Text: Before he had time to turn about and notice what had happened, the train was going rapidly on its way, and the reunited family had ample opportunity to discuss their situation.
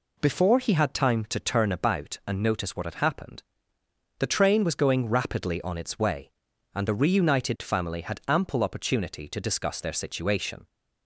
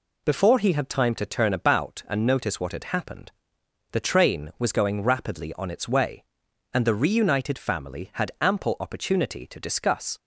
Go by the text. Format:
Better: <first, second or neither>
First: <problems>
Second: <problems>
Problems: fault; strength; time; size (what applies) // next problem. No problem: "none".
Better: first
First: none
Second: stops before "their situation"; at 10.1 s